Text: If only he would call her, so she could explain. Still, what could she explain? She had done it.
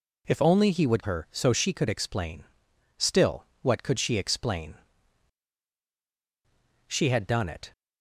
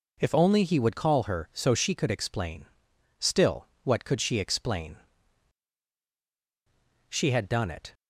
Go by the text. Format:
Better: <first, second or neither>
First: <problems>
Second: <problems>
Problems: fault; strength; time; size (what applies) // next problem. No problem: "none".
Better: second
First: skips "call"; at 1.0 s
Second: none